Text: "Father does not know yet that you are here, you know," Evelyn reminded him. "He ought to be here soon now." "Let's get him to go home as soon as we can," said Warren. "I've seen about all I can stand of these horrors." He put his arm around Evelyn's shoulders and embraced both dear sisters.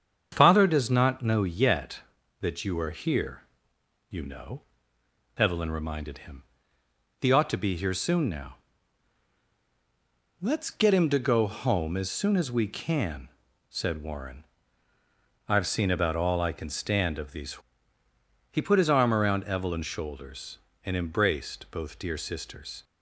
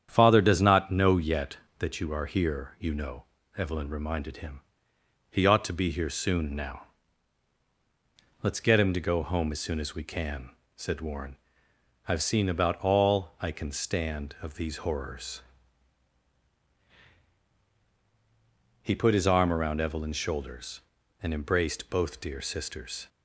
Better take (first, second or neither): second